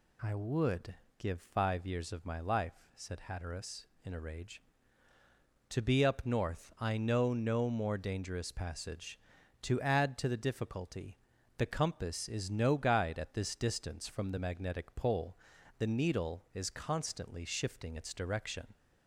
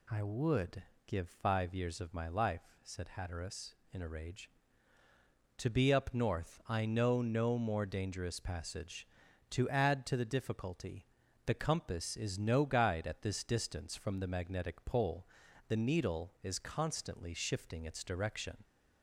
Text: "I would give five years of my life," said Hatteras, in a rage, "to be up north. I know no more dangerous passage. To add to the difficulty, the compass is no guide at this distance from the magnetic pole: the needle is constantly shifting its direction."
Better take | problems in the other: neither | pauses between "would" and "give"; slight; the same in both

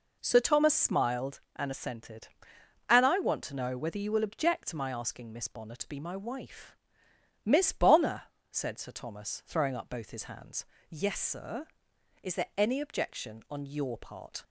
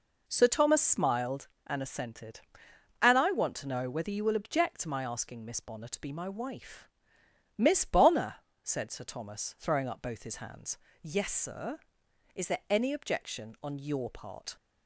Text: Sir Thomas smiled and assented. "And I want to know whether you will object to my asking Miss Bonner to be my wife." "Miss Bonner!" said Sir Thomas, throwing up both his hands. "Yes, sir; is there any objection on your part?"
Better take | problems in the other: neither | none

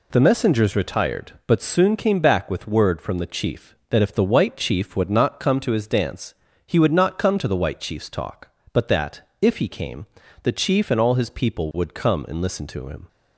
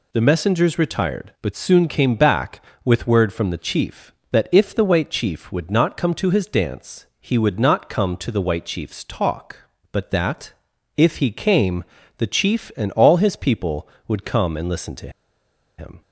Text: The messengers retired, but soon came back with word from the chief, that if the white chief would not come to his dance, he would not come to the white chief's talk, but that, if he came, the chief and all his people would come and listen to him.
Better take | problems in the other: first | pauses between "to" and "him"; noticeable; at 15.0 s; 0.69 s long

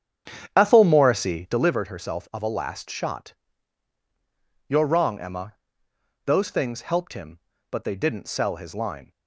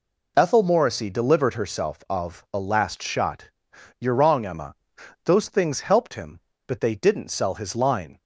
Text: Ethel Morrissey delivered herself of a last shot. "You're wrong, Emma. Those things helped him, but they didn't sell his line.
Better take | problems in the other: second | starts louder than the rest; strong; until 1.8 s; 8.5 dB

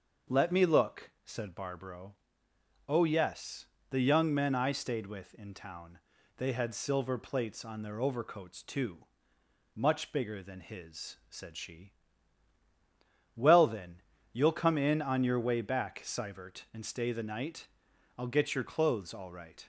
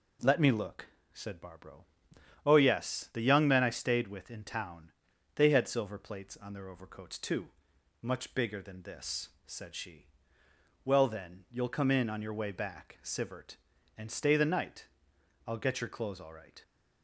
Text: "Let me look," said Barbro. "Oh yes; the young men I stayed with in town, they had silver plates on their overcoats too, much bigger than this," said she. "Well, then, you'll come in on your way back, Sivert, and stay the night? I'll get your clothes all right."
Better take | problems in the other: second | starts louder than the rest; until 1.4 s; 6.5 dB // says "his" for "this"; at 10.6 s

